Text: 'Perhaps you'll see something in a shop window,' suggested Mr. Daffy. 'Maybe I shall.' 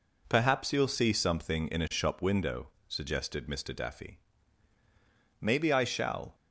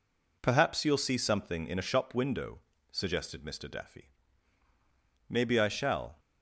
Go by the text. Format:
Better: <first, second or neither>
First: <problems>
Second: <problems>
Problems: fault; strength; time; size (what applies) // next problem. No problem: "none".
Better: neither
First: none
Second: none